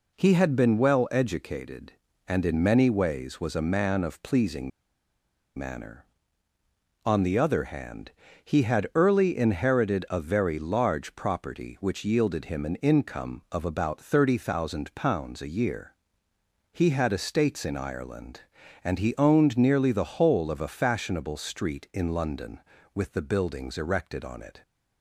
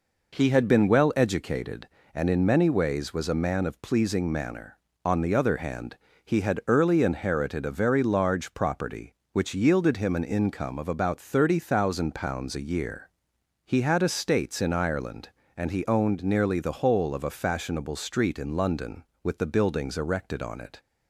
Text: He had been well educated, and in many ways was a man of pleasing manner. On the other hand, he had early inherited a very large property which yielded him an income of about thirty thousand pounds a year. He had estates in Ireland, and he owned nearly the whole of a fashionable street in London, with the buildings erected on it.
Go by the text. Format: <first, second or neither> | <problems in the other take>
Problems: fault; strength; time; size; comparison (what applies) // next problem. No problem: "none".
second | pauses between "pleasing" and "manner"; noticeable; at 4.7 s; 0.86 s long